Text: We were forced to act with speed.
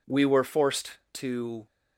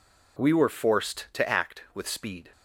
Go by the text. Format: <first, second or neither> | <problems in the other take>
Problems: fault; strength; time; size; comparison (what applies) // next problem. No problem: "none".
second | stops before "act with speed"; at 1.6 s